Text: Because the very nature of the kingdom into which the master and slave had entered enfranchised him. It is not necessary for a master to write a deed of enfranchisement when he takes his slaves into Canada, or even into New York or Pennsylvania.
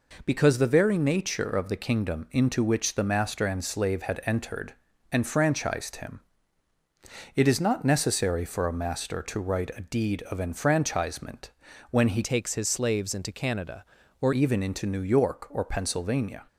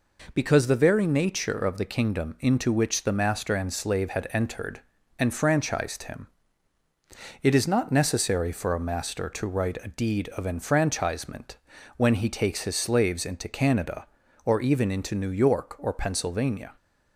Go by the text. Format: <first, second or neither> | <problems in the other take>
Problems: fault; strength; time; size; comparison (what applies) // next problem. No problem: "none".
second | pauses between "entered" and "enfranchised"; at 4.7 s; 0.38 s long; also in the second // pauses between "enfranchisement" and "when"; at 11.4 s; 0.40 s long; also in the second // changes voice from "takes" to "or"; from 12.2 to 14.3 s; 2.1 s long